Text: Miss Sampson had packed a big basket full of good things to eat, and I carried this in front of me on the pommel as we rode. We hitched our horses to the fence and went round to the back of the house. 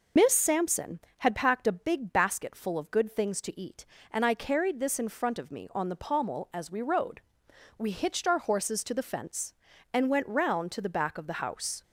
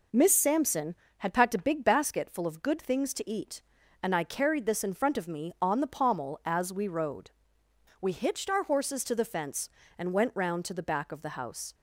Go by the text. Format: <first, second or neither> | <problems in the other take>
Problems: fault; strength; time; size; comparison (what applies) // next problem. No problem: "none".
second | loses the start of "Miss"; at 0.1 s; 75 ms